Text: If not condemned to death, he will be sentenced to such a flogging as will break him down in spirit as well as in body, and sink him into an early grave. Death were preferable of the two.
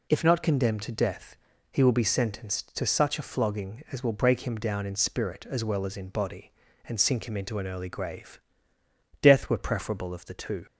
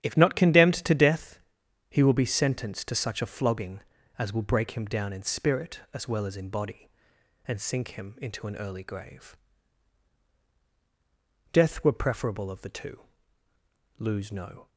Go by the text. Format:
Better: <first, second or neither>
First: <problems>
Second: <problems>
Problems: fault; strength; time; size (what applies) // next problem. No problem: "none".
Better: first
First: none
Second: starts louder than the rest; strong; until 1.0 s; 10.5 dB // goes on to say "Lose no"; noticeable; from 13.9 s on; 0.70 s long